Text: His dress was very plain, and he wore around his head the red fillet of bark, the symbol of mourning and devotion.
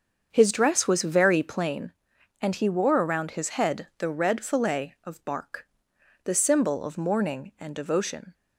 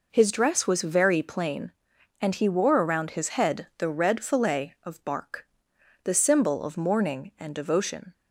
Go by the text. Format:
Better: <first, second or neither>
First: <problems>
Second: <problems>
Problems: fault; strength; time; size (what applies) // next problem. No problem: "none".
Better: second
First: starts louder than the rest; until 1.8 s; 7 dB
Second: none